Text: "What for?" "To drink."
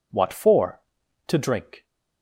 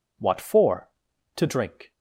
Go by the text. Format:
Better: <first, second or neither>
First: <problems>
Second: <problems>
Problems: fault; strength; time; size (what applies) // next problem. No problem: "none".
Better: neither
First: none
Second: none